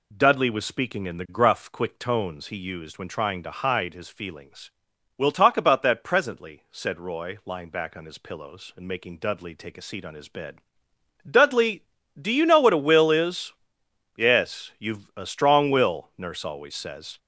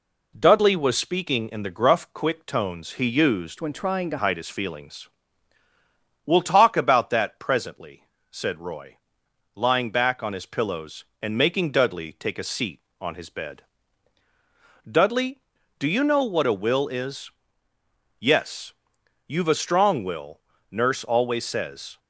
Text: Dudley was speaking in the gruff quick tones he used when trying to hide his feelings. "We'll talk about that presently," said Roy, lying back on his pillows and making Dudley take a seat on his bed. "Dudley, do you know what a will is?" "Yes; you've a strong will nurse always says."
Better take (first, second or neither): first